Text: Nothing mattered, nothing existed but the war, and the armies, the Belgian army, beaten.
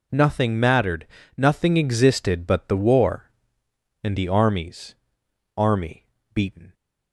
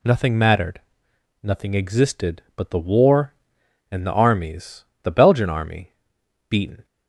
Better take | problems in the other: second | skips "the Belgian"; at 5.2 s

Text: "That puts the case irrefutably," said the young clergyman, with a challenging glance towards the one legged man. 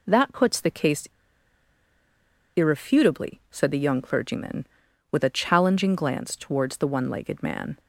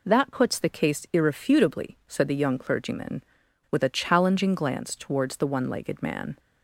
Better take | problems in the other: second | pauses between "case" and "irrefutably"; strong; at 1.0 s; 1.4 s long

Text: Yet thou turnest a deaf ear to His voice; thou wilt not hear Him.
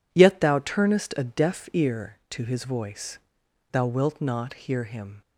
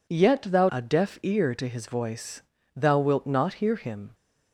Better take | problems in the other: first | skips "turnest"; at 0.6 s

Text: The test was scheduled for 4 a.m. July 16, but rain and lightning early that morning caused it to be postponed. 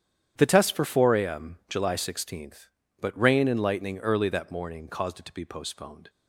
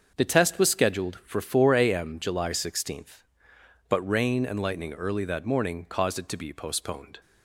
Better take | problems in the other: second | starts louder than the rest; strong; until 1.3 s; 9.5 dB; also in the second // skips "was scheduled"; at 0.7 s

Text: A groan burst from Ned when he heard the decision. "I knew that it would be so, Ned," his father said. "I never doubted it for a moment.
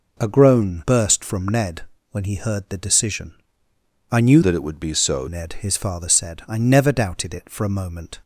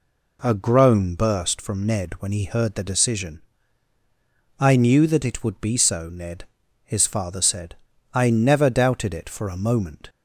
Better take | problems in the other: second | pauses between "Ned" and "when"; slight; at 1.8 s; 0.26 s long // changes voice from "that" to "so"; from 4.4 to 5.2 s; 0.8 s long

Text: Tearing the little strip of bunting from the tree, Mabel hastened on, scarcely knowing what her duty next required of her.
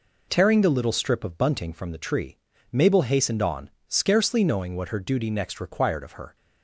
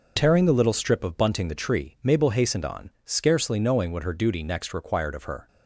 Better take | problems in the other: first | skips "from"; at 1.4 s

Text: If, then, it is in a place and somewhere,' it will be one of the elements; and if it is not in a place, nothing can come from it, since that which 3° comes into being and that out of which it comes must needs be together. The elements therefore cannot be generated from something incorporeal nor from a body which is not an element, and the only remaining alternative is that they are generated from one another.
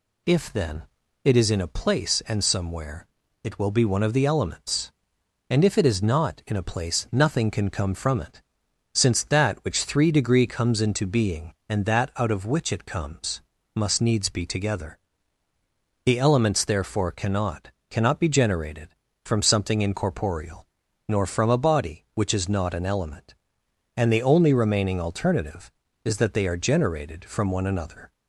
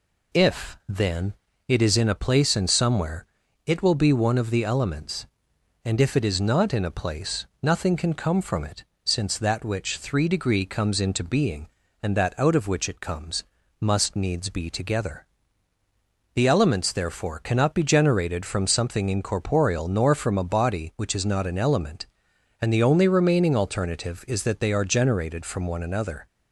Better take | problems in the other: second | pauses between "comes" and "must"; slight; at 13.4 s; 0.32 s long; slight in the second // says "cannot" twice; at 17.8 s // pauses between "incorporeal" and "nor"; at 20.6 s; 0.40 s long

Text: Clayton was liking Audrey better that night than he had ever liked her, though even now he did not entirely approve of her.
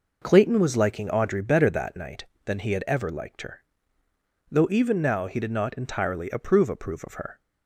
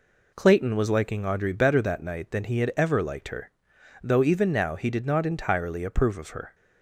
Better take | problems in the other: second | says "approve" twice; at 6.6 s

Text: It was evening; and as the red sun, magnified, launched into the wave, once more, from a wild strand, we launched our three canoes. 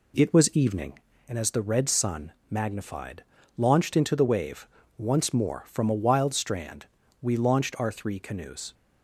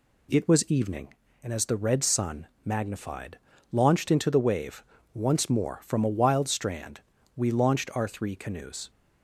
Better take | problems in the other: second | starts louder than the rest; slight; until 1.6 s; 2.5 dB

